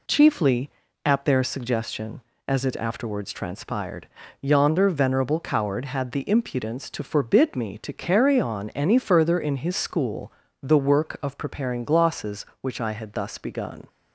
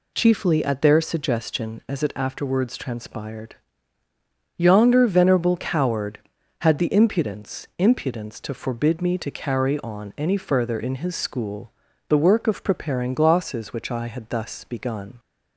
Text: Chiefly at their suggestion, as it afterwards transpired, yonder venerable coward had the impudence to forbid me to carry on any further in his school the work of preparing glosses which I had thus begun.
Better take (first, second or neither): first